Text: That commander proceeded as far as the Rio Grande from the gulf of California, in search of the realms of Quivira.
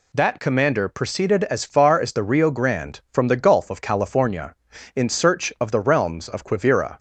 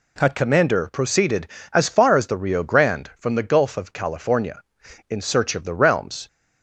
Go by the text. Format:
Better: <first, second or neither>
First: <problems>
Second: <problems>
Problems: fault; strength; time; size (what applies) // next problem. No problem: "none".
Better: first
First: none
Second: stops before "of Quivira"; at 6.2 s